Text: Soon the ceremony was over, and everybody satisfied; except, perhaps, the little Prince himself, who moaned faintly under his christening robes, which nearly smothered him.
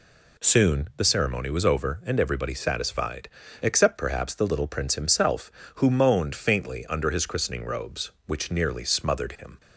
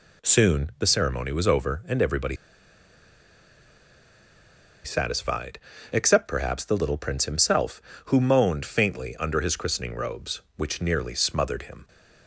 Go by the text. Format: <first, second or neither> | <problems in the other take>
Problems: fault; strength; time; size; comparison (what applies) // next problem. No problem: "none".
first | pauses between "everybody" and "satisfied"; strong; at 2.3 s; 2.4 s long